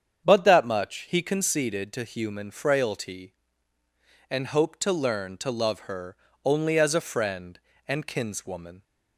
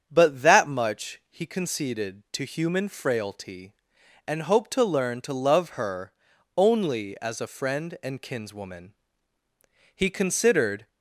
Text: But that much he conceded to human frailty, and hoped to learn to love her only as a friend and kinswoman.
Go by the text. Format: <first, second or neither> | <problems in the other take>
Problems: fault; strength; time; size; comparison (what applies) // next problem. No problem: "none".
first | starts louder than the rest; strong; until 1.1 s; 8 dB; strong in the first // pauses between "her" and "only"; at 6.1 s; 0.44 s long; slight in the first // goes on to say "He considered"; noticeable; from 9.9 s on; 0.92 s long